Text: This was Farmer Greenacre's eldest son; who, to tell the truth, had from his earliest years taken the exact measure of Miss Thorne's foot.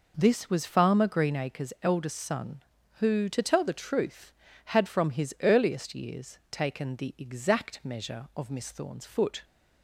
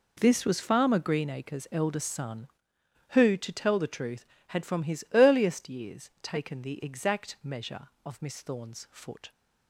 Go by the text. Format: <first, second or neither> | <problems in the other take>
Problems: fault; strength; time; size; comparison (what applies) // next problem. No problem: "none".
neither | none